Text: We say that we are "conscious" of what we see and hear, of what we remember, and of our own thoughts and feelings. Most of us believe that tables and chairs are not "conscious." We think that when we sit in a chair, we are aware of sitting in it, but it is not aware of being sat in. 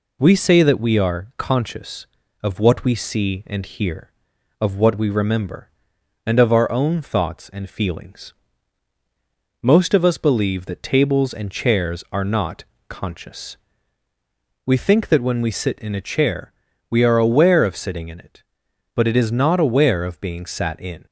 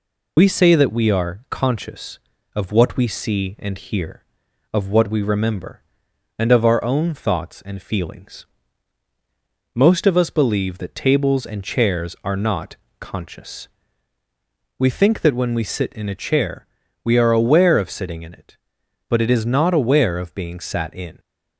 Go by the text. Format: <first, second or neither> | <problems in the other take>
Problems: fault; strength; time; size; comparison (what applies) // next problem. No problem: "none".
first | loses the start of "We"; at 0.3 s; 45 ms // pauses between "not" and "conscious"; slight; at 12.7 s; 0.23 s long; slight in the first